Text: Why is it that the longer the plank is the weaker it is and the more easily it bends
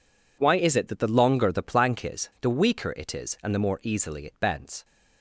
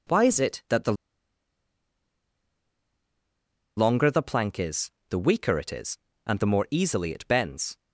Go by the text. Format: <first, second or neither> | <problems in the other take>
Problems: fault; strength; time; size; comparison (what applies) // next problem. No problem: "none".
first | pauses between "the" and "longer"; strong; at 0.9 s; 2.8 s long // pauses between "is" and "the"; slight; at 4.8 s; 0.22 s long